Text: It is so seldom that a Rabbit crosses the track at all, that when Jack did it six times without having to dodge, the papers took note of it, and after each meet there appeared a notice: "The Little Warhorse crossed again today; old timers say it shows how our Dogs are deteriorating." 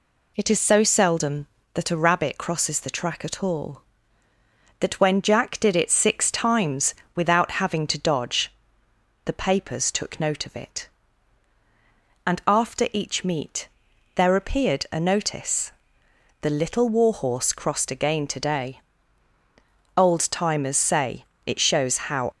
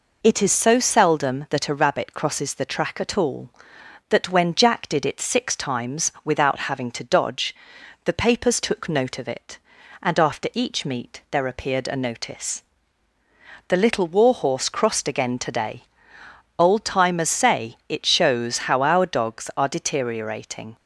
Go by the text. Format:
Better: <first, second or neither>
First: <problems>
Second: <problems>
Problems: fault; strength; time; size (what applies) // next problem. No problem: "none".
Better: second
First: pauses between "times" and "without"; slight; at 6.9 s; 0.18 s long // pauses between "meet" and "there"; noticeable; at 13.6 s; 0.48 s long // pauses between "say" and "it"; slight; at 21.2 s; 0.20 s long // stops before "our Dogs are deteriorating"; at 22.3 s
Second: none